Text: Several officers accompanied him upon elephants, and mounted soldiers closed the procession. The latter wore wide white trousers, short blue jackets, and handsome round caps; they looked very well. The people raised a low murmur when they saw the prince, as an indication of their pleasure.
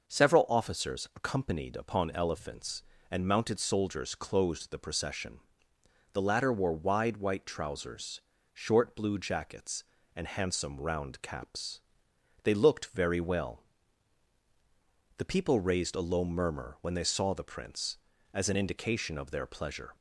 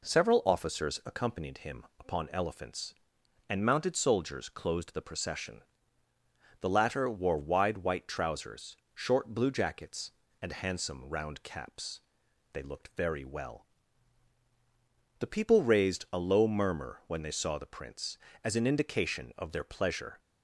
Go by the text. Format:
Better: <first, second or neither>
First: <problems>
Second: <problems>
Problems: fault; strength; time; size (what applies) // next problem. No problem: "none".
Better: second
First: skips "him"; at 1.7 s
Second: none